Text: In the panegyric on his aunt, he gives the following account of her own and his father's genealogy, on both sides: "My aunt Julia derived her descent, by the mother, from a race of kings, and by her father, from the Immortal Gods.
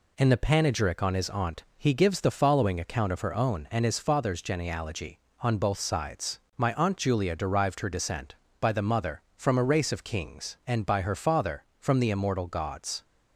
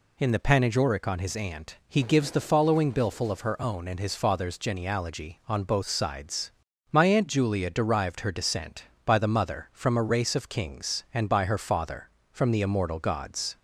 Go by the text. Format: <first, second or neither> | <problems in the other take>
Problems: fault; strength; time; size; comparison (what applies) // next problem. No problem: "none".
first | says "billful" for "account"; at 2.9 s